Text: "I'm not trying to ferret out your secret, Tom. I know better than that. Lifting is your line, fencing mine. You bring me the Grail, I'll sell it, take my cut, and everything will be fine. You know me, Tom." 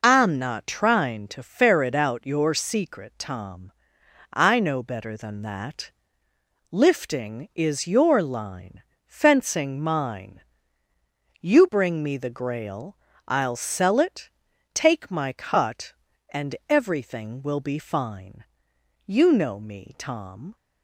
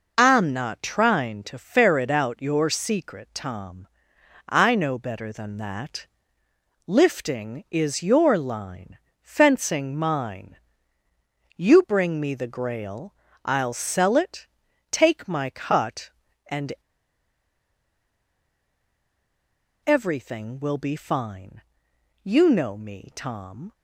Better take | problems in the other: first | pauses between "and" and "everything"; strong; at 16.7 s; 3.1 s long

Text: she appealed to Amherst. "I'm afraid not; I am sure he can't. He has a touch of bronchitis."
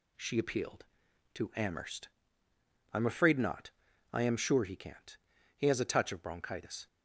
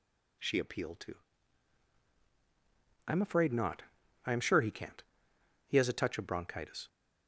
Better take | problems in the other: first | skips "Amherst"; at 2.1 s

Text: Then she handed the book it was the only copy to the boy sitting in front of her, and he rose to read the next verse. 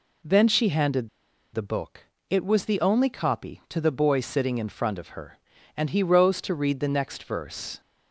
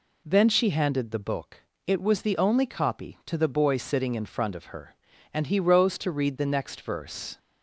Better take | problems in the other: second | pauses between "handed" and "the"; at 1.0 s; 0.45 s long // pauses between "book" and "it"; slight; at 2.0 s; 0.24 s long; slight in the second

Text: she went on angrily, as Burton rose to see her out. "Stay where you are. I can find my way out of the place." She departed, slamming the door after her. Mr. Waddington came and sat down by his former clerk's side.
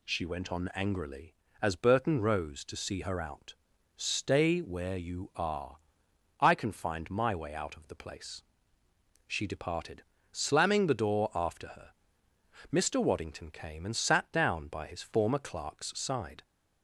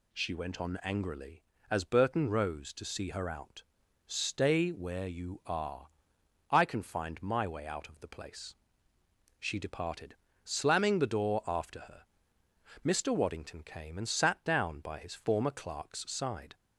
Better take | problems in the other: neither | none

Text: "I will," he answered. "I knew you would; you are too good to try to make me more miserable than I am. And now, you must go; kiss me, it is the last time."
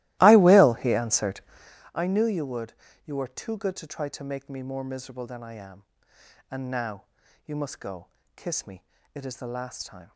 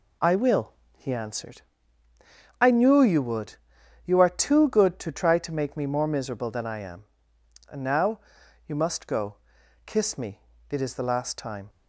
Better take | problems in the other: second | starts louder than the rest; strong; until 1.8 s; 17.5 dB

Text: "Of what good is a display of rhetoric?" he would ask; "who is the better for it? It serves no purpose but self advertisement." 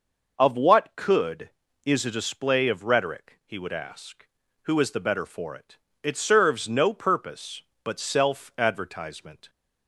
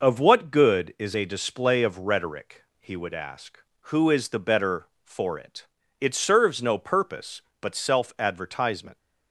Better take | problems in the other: second | says "could" for "good"; at 0.9 s

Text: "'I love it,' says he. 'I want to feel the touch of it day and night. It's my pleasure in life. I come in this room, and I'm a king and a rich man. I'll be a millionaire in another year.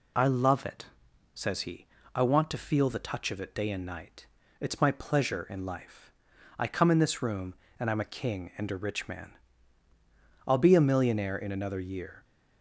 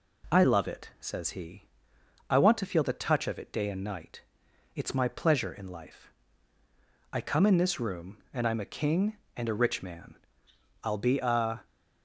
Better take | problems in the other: first | stops before "millionaire in another year"; at 11.6 s

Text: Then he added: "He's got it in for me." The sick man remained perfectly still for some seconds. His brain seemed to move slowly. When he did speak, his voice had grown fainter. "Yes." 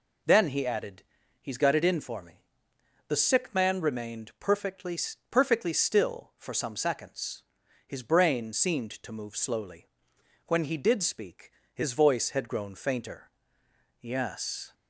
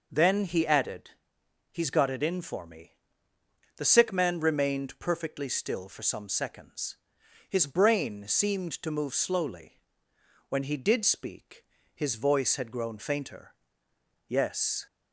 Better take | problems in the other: second | says "perfectly" twice; at 5.2 s

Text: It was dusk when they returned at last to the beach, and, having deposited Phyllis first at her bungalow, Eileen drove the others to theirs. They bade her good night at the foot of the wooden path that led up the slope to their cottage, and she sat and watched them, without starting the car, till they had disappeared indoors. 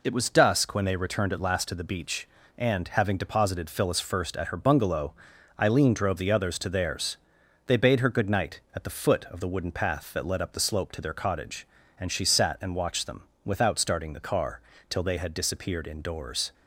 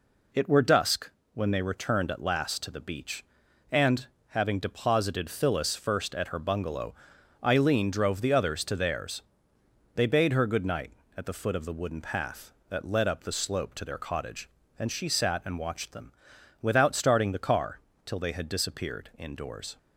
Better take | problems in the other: first | says "were" for "was"; at 0.4 s // pauses between "dusk" and "when"; slight; at 1.0 s; 0.24 s long

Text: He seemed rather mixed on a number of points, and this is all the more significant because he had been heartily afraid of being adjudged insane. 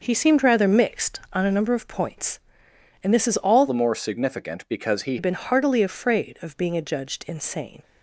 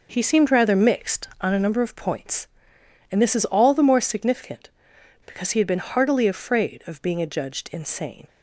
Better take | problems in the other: second | changes voice from "the" to "he"; from 3.6 to 5.1 s; 1.5 s long

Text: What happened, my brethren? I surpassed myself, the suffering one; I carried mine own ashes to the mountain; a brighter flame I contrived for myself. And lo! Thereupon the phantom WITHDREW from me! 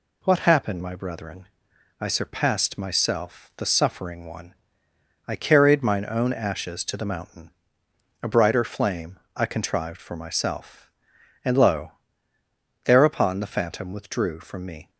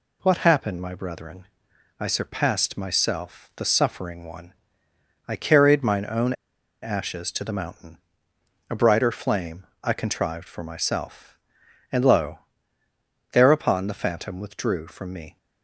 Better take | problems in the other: first | pauses between "own" and "ashes"; noticeable; at 6.3 s; 0.48 s long // pauses between "flame" and "I"; slight; at 9.6 s; 0.16 s long; slight in the first

